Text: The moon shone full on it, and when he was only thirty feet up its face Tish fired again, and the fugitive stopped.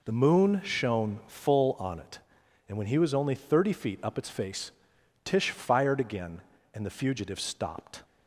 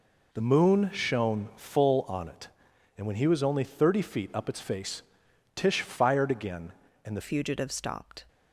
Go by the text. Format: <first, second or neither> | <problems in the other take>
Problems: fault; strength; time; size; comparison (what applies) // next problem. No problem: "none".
first | pauses between "face" and "Tish"; noticeable; at 5.0 s; 0.54 s long; noticeable in the first // changes voice at "fugitive"; from 7.2 s on; 1.0 s long